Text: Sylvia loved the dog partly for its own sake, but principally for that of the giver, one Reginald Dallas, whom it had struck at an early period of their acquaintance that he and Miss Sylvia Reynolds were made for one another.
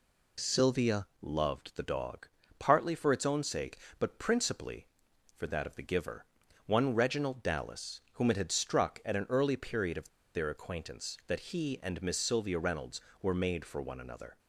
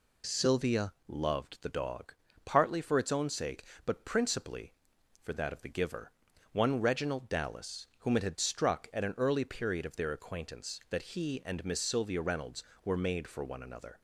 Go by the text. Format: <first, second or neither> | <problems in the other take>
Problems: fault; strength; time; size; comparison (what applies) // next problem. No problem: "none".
second | pauses between "Sylvia" and "loved"; slight; at 1.0 s; 0.16 s long; slight in the second // pauses between "dog" and "partly"; slight; at 2.2 s; 0.30 s long; slight in the second // pauses between "of" and "their"; slight; at 10.0 s; 0.28 s long